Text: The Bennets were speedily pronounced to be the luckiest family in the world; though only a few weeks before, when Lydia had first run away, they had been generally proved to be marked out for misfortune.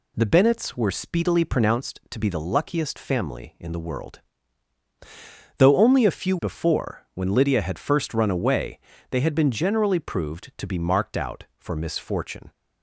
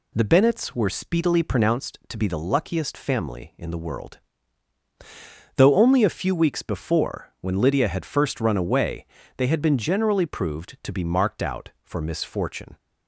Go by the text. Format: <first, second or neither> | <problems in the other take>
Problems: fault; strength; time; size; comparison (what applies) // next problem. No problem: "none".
second | skips "weeks"; at 6.3 s